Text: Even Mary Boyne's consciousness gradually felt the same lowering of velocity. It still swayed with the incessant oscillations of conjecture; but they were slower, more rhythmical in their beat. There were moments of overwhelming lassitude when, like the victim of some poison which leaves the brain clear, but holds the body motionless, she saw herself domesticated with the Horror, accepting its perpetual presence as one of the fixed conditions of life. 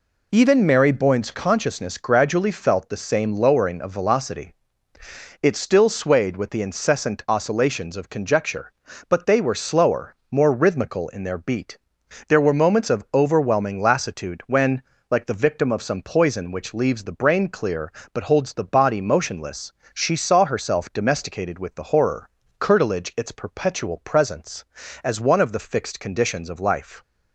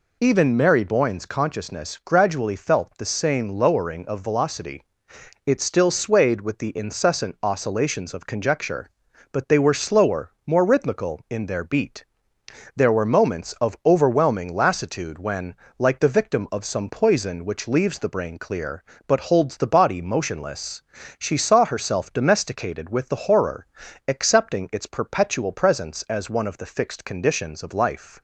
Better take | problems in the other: second | says "curtilage" for "accepting"; at 22.5 s

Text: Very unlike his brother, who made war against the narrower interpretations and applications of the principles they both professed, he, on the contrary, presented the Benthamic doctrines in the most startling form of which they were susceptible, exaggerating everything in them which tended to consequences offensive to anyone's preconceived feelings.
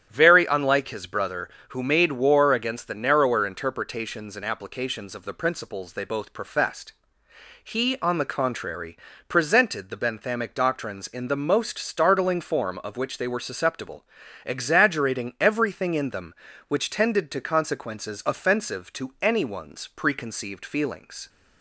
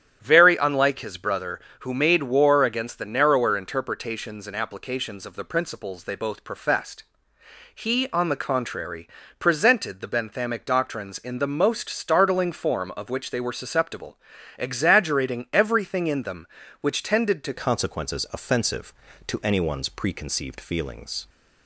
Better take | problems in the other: first | starts louder than the rest; strong; until 1.2 s; 9 dB; strong in the first // changes voice at "consequences"; from 17.5 s on; 3.7 s long

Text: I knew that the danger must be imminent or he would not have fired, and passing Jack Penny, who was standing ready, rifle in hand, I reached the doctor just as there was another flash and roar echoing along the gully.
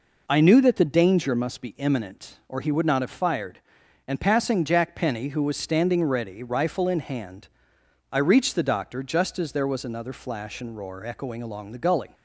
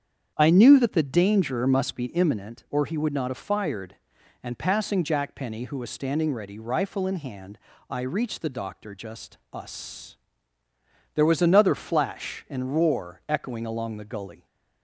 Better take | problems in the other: first | starts louder than the rest; strong; until 1.3 s; 8 dB // says "us" for "as"; at 9.5 s

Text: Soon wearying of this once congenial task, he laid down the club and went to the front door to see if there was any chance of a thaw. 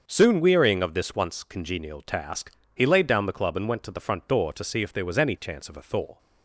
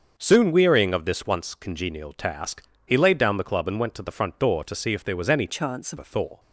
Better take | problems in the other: first | starts louder than the rest; until 1.1 s; 6.5 dB; also in the first // changes voice from "chance" to "of"; from 5.4 to 5.9 s; 0.5 s long

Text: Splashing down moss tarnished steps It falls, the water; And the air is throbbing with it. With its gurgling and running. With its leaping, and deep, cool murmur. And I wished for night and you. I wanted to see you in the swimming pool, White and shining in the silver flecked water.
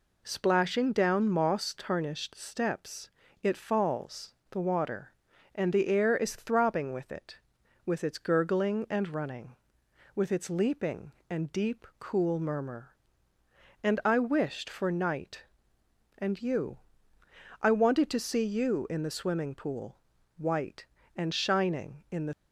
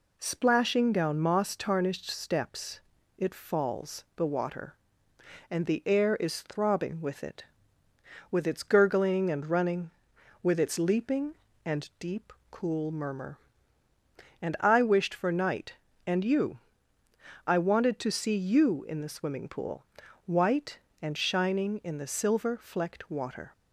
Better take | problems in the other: second | pauses between "steps" and "It"; slight; at 3.1 s; 0.30 s long; slight in the second // stops before "silver flecked water"; at 22.3 s

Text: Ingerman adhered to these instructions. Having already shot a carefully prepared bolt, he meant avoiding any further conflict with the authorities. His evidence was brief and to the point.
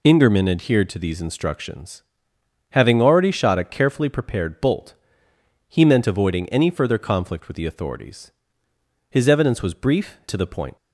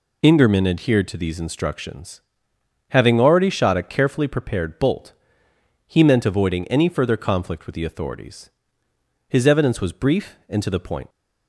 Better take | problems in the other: second | skips "and"; at 10.2 s

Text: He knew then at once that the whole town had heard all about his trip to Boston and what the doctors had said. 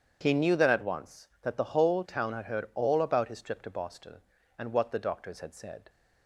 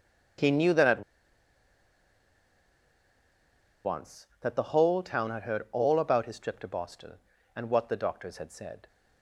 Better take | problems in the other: first | starts louder than the rest; strong; until 4.2 s; 8 dB; strong in the first // pauses between "at" and "once"; strong; at 1.0 s; 2.8 s long

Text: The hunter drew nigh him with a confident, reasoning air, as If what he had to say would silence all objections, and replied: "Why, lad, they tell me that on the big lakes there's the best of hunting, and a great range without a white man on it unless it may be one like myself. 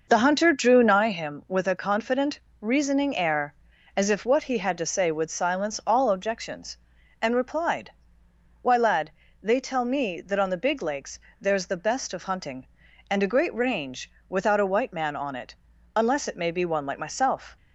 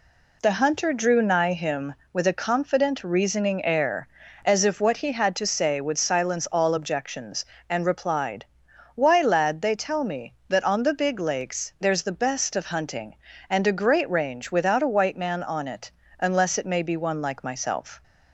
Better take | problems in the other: second | starts louder than the rest; noticeable; until 1.2 s; 6 dB // pauses between "lakes" and "there's"; slight; at 11.1 s; 0.22 s long // pauses between "range" and "without"; slight; at 14.0 s; 0.20 s long // pauses between "it" and "unless"; at 15.5 s; 0.40 s long; slight in the second

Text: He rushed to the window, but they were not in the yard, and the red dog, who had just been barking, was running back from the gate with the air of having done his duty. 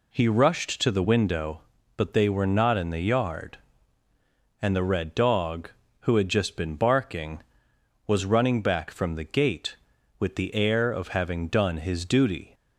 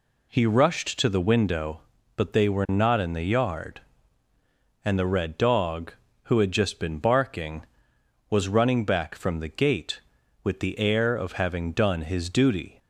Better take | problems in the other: neither | none

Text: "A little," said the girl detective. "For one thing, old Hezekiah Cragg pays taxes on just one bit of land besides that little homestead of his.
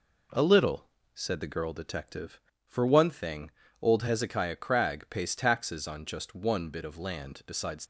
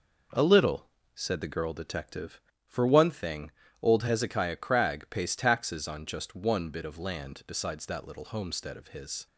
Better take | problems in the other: second | stops before "that little homestead of his"; at 7.8 s

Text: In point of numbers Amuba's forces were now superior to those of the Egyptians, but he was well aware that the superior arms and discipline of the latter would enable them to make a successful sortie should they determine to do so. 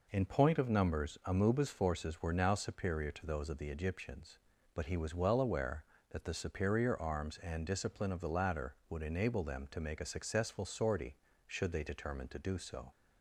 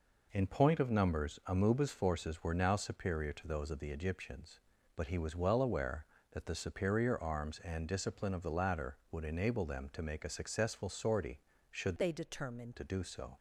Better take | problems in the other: first | changes voice from "they" to "determine"; from 11.9 to 12.7 s; 0.8 s long

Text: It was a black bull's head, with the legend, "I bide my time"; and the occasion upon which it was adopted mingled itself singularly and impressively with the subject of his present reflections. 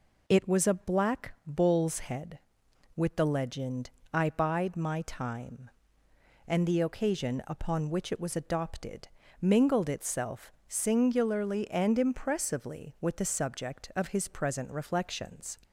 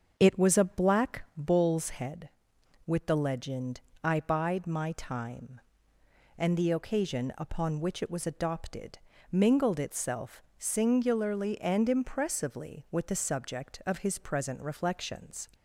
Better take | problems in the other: first | starts louder than the rest; until 1.6 s; 6.5 dB // pauses between "adopted" and "mingled"; slight; at 8.9 s; 0.34 s long; slight in the first // pauses between "itself" and "singularly"; slight; at 10.4 s; 0.16 s long; slight in the first

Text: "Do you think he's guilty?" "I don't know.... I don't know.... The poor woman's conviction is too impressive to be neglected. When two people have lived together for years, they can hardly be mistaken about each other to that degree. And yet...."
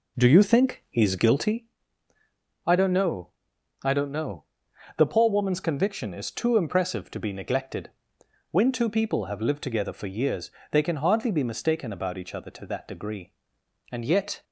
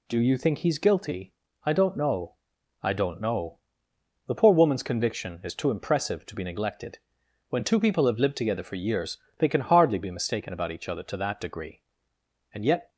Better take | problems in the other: second | starts louder than the rest; until 1.6 s; 3.5 dB

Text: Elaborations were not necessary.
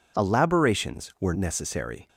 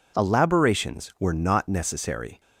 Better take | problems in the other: second | skips "not"; at 1.3 s

